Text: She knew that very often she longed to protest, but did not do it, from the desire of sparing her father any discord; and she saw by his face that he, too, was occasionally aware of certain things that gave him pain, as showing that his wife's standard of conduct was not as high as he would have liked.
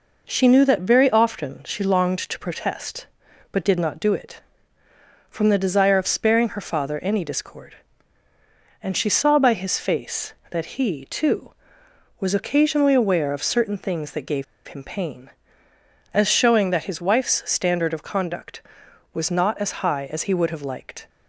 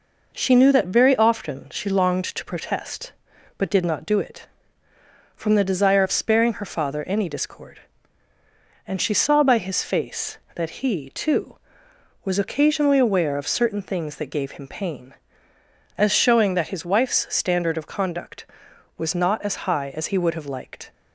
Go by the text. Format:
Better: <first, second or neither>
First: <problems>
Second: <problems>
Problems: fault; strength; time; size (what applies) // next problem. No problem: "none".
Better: second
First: pauses between "gave" and "him"; slight; at 14.4 s; 0.23 s long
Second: none